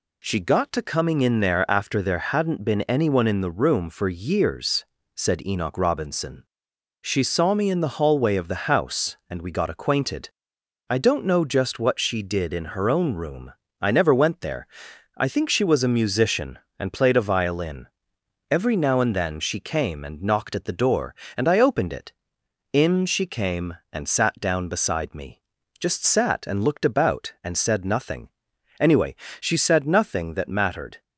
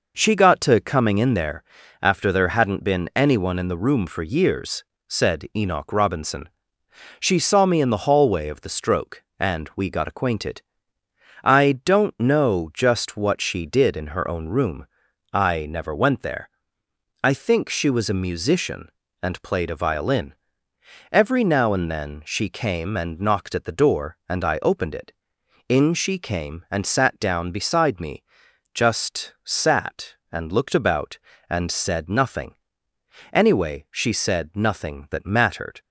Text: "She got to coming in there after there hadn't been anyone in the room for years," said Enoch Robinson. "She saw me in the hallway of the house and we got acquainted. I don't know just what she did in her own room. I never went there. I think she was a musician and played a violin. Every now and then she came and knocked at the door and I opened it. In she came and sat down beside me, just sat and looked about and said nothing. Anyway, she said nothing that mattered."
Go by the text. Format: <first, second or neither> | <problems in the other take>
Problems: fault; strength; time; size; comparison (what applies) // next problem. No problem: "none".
first | pauses between "there" and "after"; at 1.6 s; 0.40 s long // says "stroke" for "house"; at 8.6 s